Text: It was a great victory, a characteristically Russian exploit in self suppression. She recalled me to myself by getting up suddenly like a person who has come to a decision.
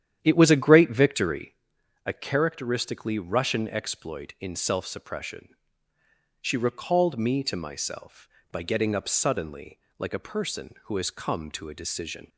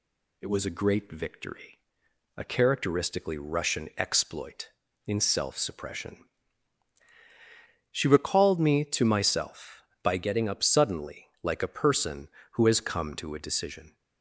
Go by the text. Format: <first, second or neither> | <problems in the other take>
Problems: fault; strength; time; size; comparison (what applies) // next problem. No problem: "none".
second | starts louder than the rest; strong; until 1.6 s; 10 dB // pauses between "suddenly" and "like"; slight; at 9.7 s; 0.20 s long; slight in the second